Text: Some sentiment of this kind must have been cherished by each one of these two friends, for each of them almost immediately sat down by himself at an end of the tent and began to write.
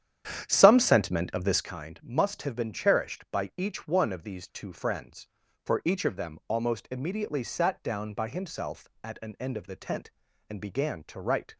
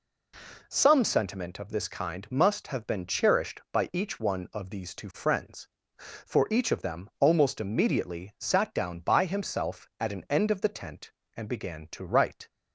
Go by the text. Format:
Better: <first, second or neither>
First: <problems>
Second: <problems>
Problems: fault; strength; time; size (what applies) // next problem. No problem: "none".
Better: second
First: starts louder than the rest; strong; until 1.7 s; 9.5 dB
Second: none